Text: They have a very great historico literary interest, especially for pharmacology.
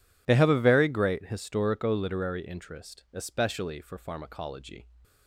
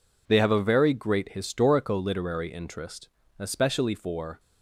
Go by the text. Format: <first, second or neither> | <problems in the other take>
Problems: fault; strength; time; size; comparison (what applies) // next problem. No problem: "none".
first | stops before "pharmacology"; at 4.3 s